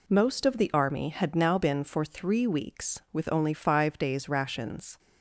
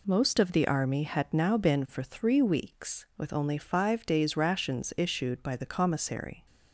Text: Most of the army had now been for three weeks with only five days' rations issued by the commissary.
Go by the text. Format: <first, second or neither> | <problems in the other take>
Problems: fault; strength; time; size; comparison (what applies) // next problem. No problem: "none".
second | stops before "issued by the commissary"; at 4.9 s